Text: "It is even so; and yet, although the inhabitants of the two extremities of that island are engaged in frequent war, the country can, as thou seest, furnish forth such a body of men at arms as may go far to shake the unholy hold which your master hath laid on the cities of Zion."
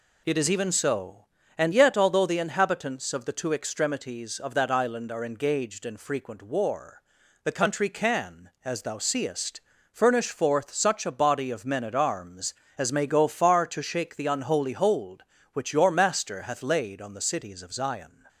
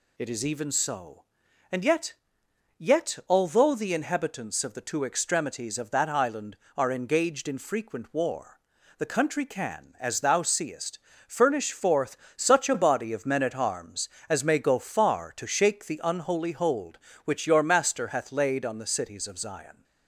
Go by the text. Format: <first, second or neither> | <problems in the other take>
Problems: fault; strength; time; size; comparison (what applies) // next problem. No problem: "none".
first | says "yet" twice; at 2.7 s // pauses between "forth" and "such"; slight; at 12.1 s; 0.22 s long